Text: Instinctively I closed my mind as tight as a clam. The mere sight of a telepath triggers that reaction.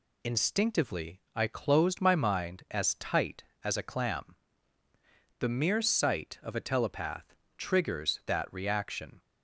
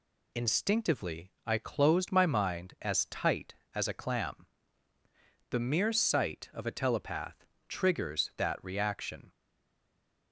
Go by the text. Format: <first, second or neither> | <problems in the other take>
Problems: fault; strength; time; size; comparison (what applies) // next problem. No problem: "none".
first | pauses between "telepath" and "triggers"; slight; at 7.4 s; 0.20 s long; slight in the first // stays silent after the last word; from 9.3 s on; 1.0 s long